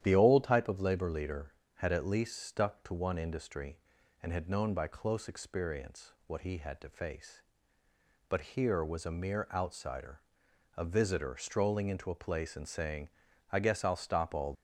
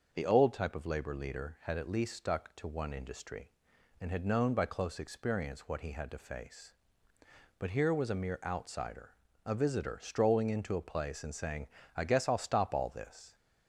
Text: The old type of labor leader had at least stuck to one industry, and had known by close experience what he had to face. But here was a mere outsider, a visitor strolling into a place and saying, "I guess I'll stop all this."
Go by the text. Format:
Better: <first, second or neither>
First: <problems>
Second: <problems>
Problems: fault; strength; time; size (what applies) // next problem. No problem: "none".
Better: second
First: starts louder than the rest; strong; until 1.0 s; 10.5 dB // stops before "this"; at 14.5 s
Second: starts louder than the rest; noticeable; until 1.1 s; 6 dB